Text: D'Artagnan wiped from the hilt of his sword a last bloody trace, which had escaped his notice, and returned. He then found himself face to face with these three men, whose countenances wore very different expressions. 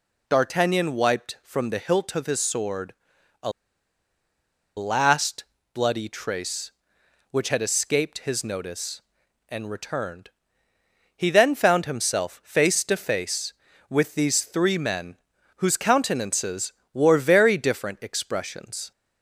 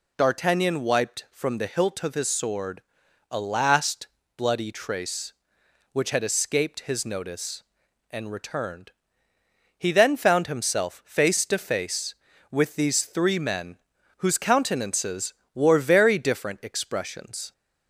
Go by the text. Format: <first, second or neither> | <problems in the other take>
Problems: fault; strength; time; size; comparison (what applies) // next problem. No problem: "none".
second | pauses between "sword" and "a"; noticeable; at 2.9 s; 0.48 s long; noticeable in the second // pauses between "a" and "last"; strong; at 3.5 s; 1.2 s long // pauses between "last" and "bloody"; slight; at 5.4 s; 0.30 s long; slight in the second // pauses between "countenances" and "wore"; slight; at 16.7 s; 0.22 s long; slight in the second